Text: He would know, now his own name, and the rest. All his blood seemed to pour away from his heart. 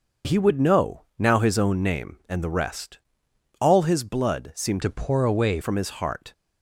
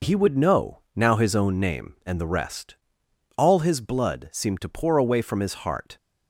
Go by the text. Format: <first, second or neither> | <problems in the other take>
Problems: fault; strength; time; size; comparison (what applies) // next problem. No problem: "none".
second | changes voice from "to" to "away"; from 4.8 to 5.6 s; 0.8 s long